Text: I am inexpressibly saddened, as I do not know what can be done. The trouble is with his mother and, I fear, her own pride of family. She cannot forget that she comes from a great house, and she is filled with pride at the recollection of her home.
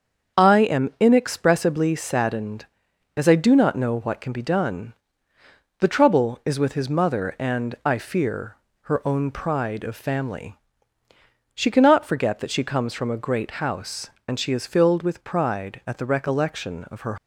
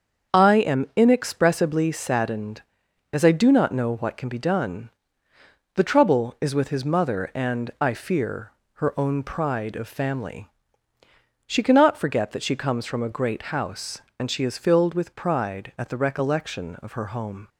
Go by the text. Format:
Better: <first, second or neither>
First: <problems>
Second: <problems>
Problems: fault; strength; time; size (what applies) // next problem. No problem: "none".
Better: second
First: starts louder than the rest; until 1.4 s; 7 dB // stops before "home"; at 17.1 s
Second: starts louder than the rest; until 1.4 s; 7 dB